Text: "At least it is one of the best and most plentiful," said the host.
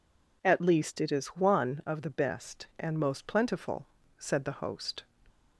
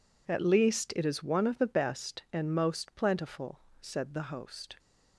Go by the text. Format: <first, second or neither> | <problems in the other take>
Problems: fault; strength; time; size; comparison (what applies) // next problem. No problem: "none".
neither | none